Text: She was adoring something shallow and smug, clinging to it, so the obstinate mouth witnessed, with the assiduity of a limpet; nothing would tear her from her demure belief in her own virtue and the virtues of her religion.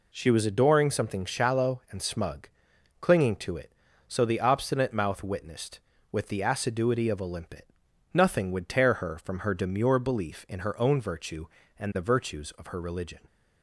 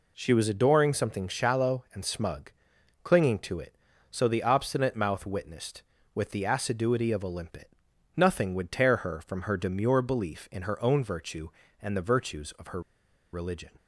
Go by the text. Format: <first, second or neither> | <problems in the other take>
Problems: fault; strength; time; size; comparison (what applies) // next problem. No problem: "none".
first | pauses between "her" and "religion"; noticeable; at 12.8 s; 0.52 s long